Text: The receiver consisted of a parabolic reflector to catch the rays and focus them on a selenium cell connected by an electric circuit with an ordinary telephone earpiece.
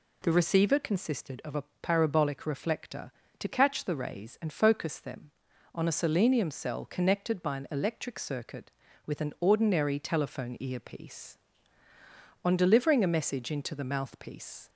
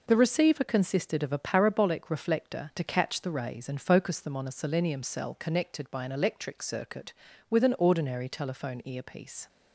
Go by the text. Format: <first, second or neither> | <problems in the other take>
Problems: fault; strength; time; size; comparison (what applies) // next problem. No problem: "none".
second | pauses between "a" and "parabolic"; slight; at 1.6 s; 0.16 s long // goes on to say "On delivering a message into the mouthpiece"; strong; from 12.4 s on; 2.2 s long